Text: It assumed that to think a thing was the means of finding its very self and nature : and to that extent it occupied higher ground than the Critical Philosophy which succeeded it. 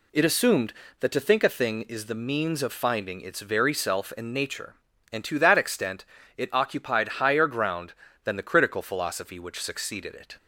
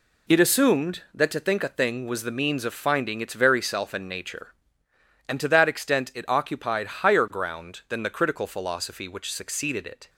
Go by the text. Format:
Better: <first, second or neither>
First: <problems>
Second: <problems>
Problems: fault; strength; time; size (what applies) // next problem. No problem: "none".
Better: second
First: says "is" for "was"; at 1.8 s // pauses between "extent" and "it"; slight; at 6.0 s; 0.30 s long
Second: none